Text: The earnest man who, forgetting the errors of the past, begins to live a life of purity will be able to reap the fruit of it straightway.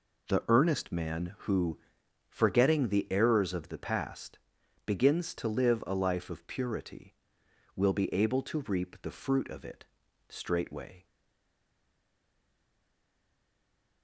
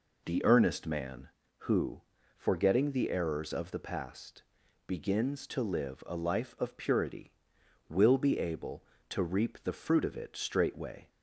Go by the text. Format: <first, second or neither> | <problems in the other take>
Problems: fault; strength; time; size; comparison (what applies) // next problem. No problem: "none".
second | pauses between "it" and "straightway"; at 9.8 s; 0.44 s long // stays silent after the last word; strong; from 11.0 s on; 3.0 s long